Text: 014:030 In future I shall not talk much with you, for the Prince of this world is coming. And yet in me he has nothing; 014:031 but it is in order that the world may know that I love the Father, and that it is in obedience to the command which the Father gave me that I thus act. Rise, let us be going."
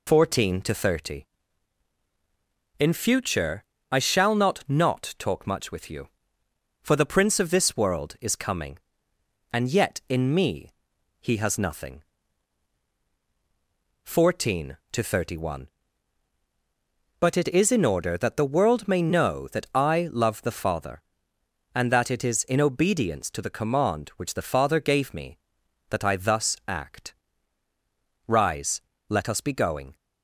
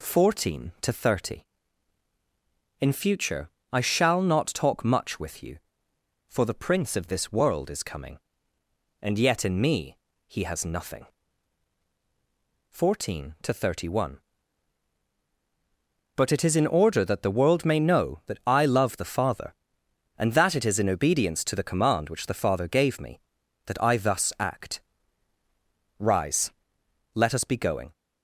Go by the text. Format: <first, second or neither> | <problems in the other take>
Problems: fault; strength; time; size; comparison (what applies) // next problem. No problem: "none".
second | pauses between "future" and "I"; slight; at 3.6 s; 0.26 s long; slight in the second // says "not" twice; at 4.6 s // pauses between "me" and "he"; noticeable; at 10.7 s; 0.50 s long; slight in the second